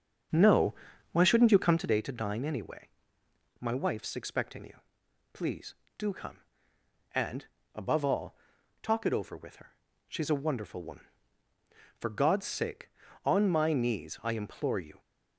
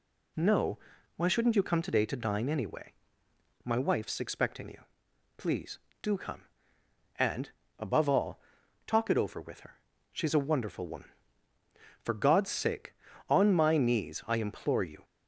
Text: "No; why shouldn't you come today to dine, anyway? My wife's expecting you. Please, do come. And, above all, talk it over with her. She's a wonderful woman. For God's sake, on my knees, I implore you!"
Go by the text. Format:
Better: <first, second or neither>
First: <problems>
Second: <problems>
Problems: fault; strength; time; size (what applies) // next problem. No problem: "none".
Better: second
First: starts louder than the rest; until 2.0 s; 7 dB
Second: none